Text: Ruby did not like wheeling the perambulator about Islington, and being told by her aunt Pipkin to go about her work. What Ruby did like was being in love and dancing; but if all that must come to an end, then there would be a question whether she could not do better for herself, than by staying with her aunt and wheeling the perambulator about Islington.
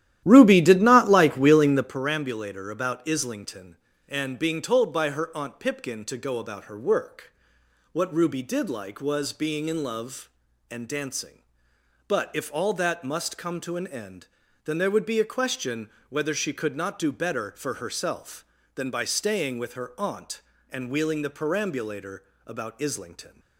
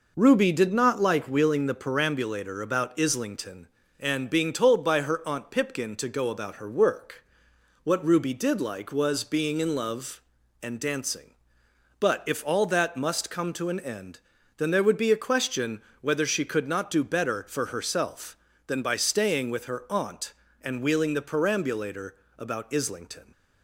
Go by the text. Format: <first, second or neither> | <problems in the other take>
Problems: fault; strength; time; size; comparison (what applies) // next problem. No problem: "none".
second | starts louder than the rest; strong; until 2.0 s; 12.5 dB // pauses between "question" and "whether"; slight; at 15.8 s; 0.18 s long; slight in the second // pauses between "perambulator" and "about"; slight; at 22.2 s; 0.24 s long; slight in the second